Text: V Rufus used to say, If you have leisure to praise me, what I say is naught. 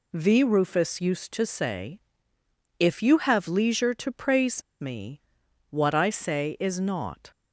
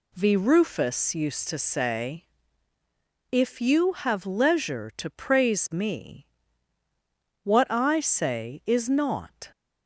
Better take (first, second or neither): second